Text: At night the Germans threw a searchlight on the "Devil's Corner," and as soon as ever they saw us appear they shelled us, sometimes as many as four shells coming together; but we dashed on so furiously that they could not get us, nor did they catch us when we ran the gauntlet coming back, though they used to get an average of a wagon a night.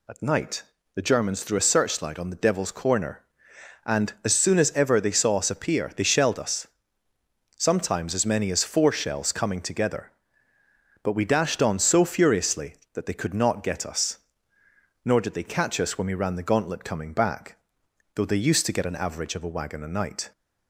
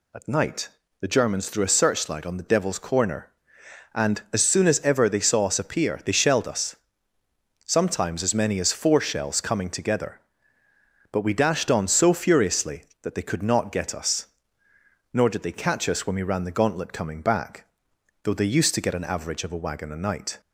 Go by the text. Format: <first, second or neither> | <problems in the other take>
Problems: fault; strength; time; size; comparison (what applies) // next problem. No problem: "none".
neither | pauses between "night" and "the"; slight; the same in both